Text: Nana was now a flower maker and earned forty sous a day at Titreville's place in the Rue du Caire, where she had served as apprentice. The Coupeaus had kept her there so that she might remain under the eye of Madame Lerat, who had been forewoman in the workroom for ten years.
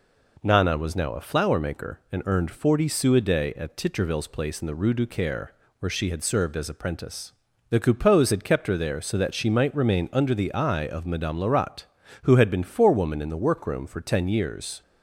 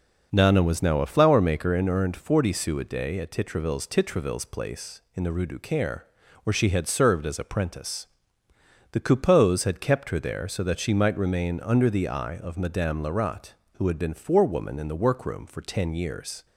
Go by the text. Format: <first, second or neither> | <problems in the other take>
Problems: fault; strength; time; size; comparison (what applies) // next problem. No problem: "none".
first | says "Titreville's" twice; at 3.8 s